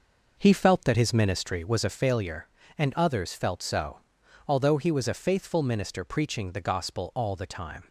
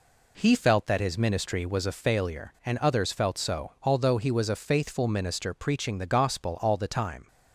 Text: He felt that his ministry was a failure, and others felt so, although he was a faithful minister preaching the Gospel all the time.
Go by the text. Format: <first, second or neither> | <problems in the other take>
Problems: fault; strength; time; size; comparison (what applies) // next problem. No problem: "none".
second | starts louder than the rest; noticeable; until 2.0 s; 5.5 dB